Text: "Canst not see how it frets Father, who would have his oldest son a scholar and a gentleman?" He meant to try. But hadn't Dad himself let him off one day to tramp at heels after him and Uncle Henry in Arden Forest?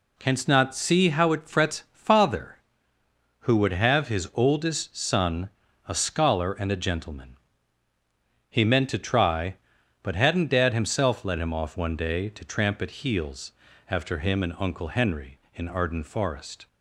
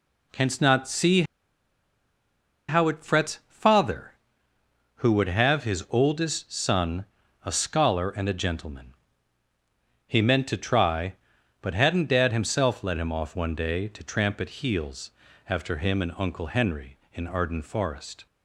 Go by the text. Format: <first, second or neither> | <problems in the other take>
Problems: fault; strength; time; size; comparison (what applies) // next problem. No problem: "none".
first | pauses between "see" and "how"; strong; at 1.2 s; 1.4 s long // pauses between "son" and "a"; at 7.0 s; 0.40 s long; also in the first // pauses between "heels" and "after"; slight; at 15.1 s; 0.36 s long; slight in the first